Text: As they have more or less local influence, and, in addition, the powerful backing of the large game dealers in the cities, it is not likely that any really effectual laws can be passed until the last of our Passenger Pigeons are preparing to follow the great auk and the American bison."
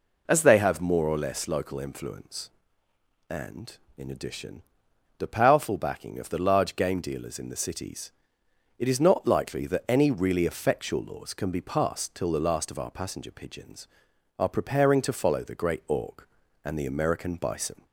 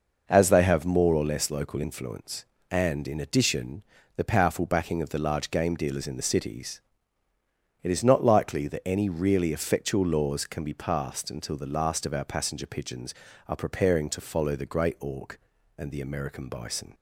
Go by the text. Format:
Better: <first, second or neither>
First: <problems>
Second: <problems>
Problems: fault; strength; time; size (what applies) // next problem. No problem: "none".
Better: second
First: says "till" for "until"; at 12.1 s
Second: none